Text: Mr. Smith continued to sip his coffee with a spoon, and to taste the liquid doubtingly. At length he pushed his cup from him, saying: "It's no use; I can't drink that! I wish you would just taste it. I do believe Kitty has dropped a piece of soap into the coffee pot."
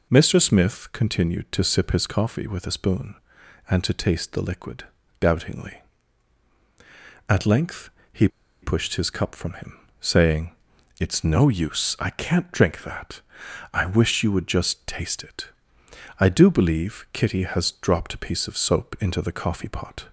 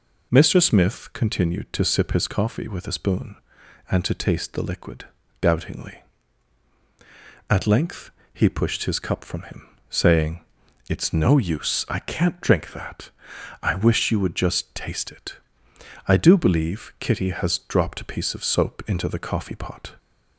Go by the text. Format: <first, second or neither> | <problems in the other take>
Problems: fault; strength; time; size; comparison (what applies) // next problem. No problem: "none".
second | pauses between "liquid" and "doubtingly"; slight; at 4.8 s; 0.34 s long; slight in the second // pauses between "length" and "he"; slight; at 7.8 s; 0.24 s long; slight in the second // pauses between "he" and "pushed"; slight; at 8.2 s; 0.34 s long